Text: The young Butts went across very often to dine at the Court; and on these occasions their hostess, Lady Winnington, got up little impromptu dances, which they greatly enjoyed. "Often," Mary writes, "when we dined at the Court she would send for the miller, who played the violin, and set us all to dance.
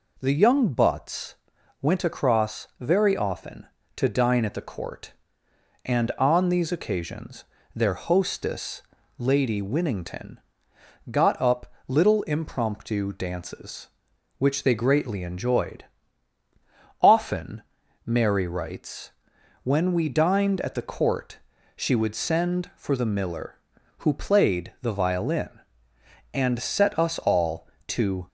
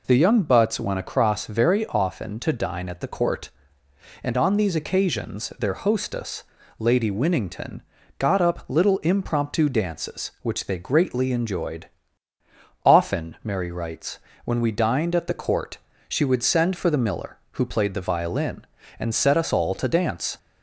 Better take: second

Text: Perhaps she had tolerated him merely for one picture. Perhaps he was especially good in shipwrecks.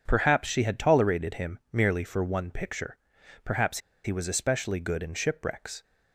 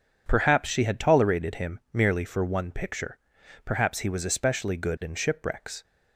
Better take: second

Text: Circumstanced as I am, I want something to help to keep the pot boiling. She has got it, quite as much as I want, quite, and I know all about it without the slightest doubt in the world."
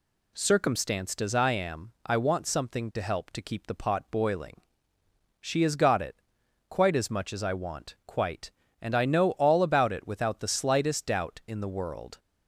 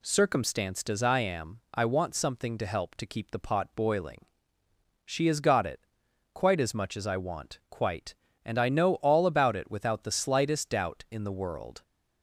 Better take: neither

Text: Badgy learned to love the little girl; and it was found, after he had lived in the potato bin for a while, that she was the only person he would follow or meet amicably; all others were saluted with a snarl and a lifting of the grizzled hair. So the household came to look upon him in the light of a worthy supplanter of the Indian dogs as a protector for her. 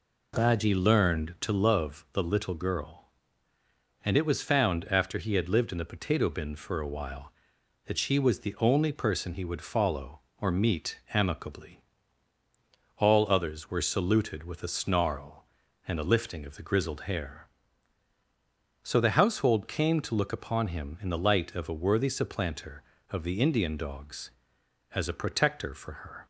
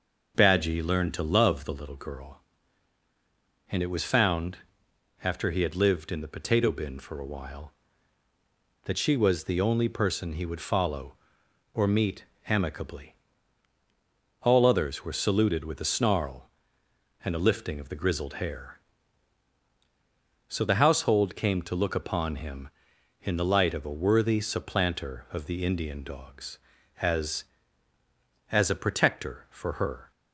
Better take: first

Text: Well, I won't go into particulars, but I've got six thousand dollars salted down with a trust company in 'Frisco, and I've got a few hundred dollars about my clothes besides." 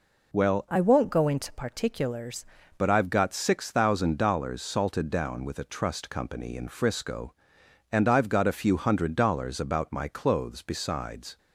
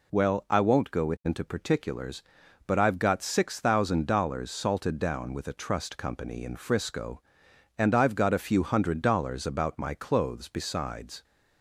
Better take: second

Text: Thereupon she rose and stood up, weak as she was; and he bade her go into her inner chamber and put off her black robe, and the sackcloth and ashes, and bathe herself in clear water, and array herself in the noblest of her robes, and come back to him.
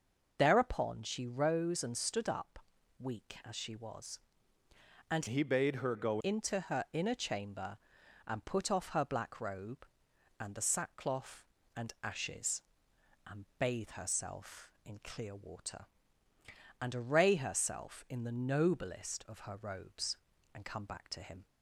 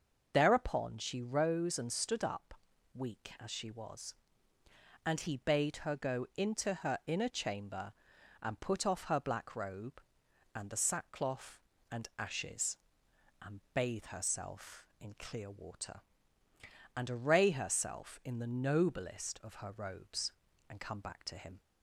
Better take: second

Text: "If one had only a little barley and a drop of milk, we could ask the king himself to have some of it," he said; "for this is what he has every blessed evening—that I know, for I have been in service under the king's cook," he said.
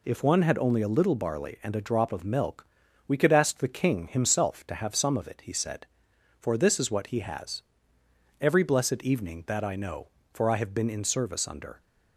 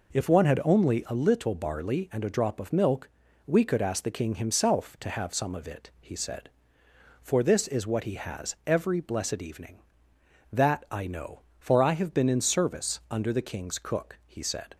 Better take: second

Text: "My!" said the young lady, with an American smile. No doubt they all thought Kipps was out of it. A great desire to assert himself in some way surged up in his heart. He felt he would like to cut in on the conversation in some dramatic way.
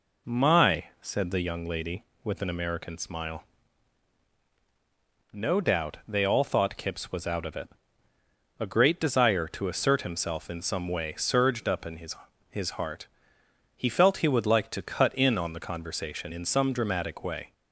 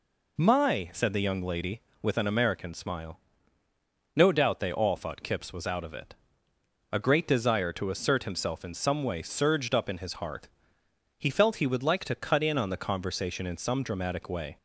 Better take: second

